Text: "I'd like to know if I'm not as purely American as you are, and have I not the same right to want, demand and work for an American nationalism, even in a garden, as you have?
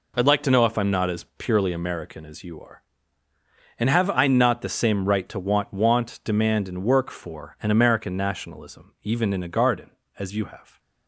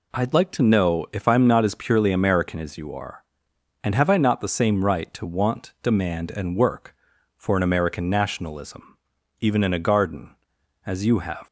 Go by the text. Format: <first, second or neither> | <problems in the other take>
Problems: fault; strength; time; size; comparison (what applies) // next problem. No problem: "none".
second | says "want" twice; at 5.7 s